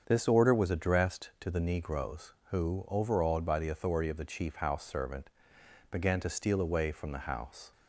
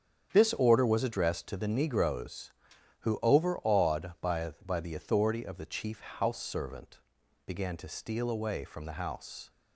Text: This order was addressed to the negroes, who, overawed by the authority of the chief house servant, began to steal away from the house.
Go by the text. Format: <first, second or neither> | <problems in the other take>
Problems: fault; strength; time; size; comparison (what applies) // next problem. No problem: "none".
first | starts louder than the rest; strong; until 1.3 s; 8 dB; strong in the first // says "by" twice; at 4.6 s